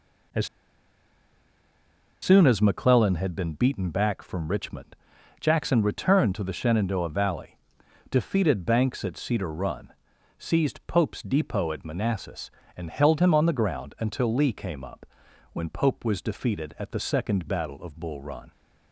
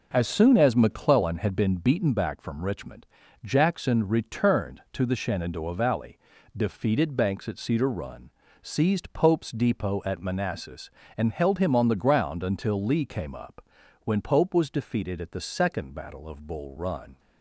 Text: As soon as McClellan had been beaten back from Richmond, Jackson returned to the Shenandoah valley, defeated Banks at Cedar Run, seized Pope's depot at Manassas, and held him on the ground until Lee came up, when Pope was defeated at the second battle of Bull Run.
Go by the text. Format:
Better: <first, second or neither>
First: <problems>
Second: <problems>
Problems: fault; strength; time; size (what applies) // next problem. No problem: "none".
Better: second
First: pauses between "As" and "soon"; strong; at 0.4 s; 1.7 s long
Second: none